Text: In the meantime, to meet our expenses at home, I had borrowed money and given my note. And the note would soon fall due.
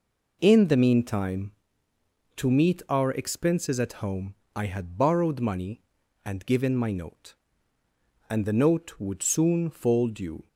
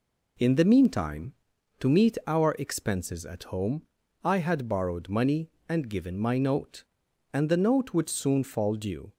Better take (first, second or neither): neither